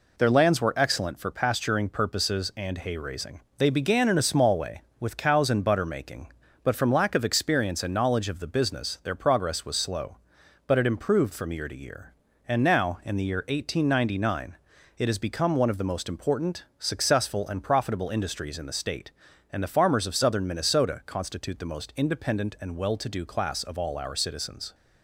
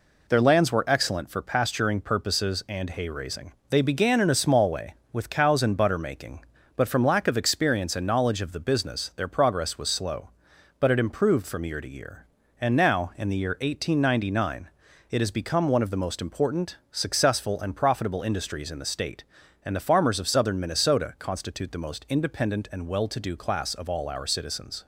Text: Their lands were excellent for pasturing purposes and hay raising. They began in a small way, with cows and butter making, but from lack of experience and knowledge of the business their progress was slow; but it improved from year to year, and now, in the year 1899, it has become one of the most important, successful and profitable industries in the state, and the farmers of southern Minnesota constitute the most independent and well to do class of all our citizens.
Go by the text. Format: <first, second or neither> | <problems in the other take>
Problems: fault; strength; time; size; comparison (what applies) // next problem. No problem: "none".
neither | none